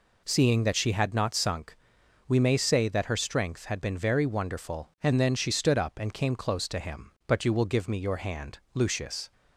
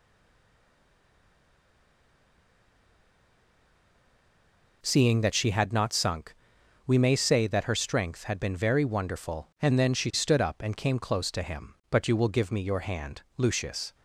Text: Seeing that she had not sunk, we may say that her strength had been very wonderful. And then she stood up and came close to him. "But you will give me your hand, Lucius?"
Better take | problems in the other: first | stays silent before the first word; strong; until 4.8 s; 4.8 s long

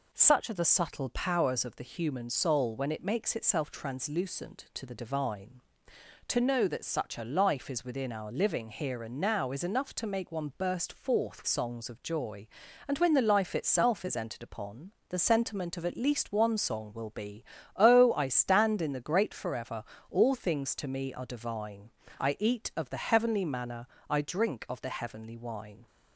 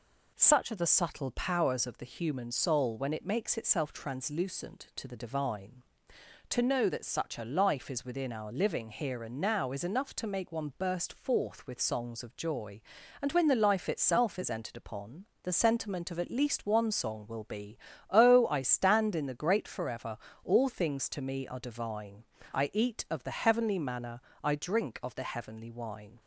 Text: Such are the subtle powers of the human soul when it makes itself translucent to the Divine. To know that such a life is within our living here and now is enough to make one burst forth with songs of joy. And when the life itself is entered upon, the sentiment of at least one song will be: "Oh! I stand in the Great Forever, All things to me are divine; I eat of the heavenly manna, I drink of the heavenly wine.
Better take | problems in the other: second | skips "with"; at 11.4 s

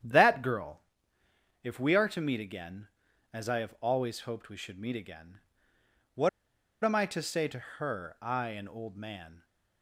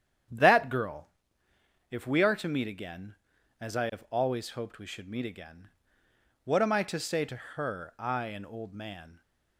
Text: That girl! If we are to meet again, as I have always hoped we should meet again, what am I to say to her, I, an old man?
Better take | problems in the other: second | starts louder than the rest; strong; until 1.8 s; 9.5 dB; strong in the second // pauses between "what" and "am"; noticeable; at 6.2 s; 0.54 s long

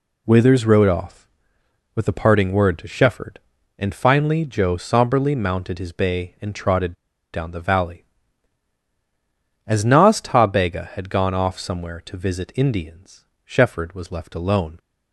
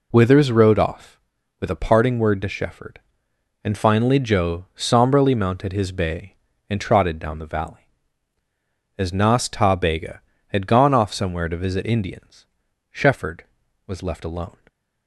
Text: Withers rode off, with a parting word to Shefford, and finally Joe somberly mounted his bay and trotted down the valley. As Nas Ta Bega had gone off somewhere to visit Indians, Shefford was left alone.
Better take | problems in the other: second | pauses between "trotted" and "down"; at 6.9 s; 0.39 s long

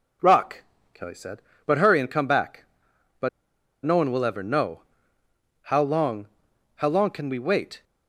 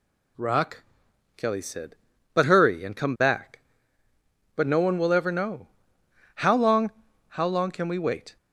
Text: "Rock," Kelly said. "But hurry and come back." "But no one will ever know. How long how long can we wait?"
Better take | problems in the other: second | pauses between "But" and "no"; noticeable; at 3.2 s; 0.56 s long // pauses between "long" and "how"; noticeable; at 6.2 s; 0.52 s long; also in the second

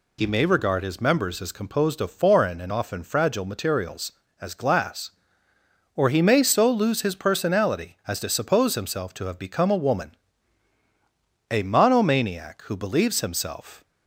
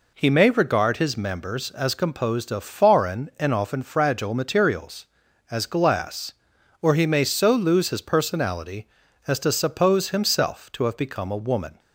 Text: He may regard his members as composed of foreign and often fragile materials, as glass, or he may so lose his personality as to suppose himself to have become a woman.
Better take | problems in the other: second | goes on to say "A monomaniac who believes himself"; strong; from 11.5 s on; 2.3 s long

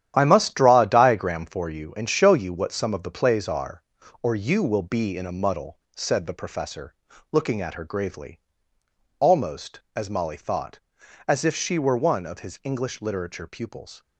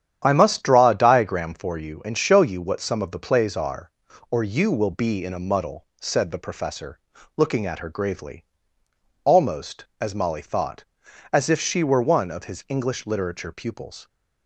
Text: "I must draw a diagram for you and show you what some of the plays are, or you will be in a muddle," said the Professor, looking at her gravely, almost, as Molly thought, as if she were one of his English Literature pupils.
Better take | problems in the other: second | gets quieter; strong; throughout; 9 dB // starts louder than the rest; strong; until 1.1 s; 10.5 dB; strong in the second

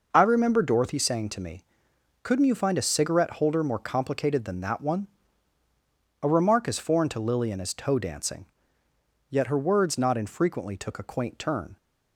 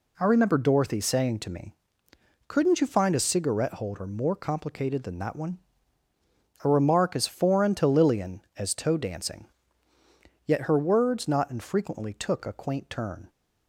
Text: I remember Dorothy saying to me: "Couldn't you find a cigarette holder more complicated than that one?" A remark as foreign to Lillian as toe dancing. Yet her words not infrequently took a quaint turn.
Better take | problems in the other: neither | none

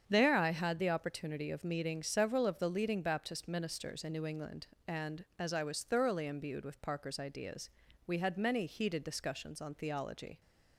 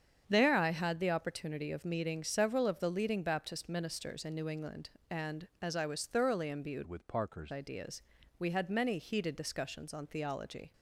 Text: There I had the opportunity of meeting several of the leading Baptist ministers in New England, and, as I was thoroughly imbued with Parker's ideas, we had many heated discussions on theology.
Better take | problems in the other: first | starts louder than the rest; strong; until 1.2 s; 7.5 dB; strong in the first // changes voice from "with" to "Parker's"; from 6.8 to 7.5 s; 0.7 s long

